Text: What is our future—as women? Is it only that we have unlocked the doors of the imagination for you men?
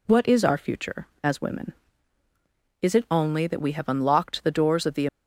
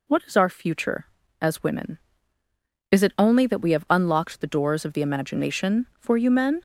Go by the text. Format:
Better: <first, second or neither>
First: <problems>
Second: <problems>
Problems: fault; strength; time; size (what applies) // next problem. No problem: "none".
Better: second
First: stops before "imagination for you men"; at 5.0 s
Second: none